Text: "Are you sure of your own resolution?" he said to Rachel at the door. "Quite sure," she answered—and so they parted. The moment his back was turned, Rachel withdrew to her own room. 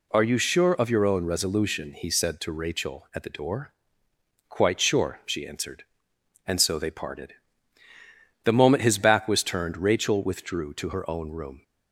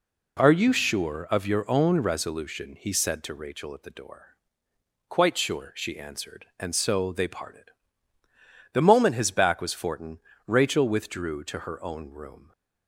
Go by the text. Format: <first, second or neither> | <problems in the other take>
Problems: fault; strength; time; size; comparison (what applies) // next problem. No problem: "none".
first | says "fortin" for "turned"; at 9.7 s